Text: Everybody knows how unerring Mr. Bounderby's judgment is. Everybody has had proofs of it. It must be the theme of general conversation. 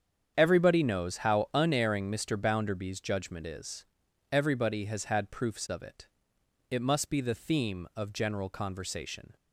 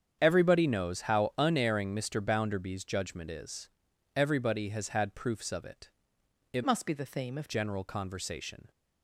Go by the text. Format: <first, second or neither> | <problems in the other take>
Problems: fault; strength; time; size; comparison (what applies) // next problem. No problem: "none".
first | starts louder than the rest; strong; until 1.2 s; 8 dB; strong in the first // changes voice from "must" to "of"; from 6.6 to 7.5 s; 0.9 s long